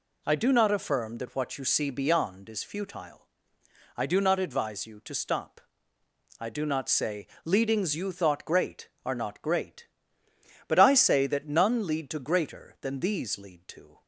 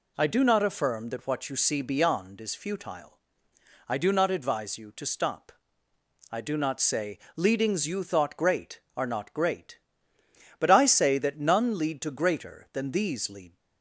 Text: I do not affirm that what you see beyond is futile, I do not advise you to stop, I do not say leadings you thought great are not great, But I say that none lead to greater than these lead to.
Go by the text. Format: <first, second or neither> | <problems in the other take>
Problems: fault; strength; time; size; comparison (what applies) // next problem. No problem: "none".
first | pauses between "say" and "leadings"; slight; at 7.1 s; 0.18 s long; slight in the first // stops before "to"; at 13.5 s